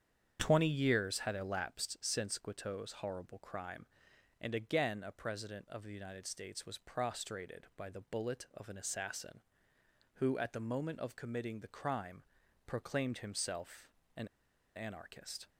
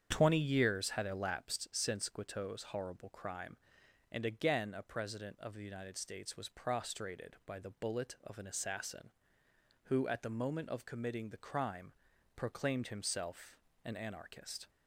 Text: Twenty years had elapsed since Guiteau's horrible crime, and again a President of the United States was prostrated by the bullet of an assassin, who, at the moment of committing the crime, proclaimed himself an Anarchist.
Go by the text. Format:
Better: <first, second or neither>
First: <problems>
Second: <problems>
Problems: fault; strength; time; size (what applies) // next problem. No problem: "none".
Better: second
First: starts louder than the rest; strong; until 1.4 s; 8 dB // pauses between "himself" and "an"; slight; at 13.8 s; 0.30 s long // pauses between "an" and "Anarchist"; noticeable; at 14.2 s; 0.50 s long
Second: starts louder than the rest; strong; until 1.1 s; 8 dB // pauses between "himself" and "an"; slight; at 13.5 s; 0.30 s long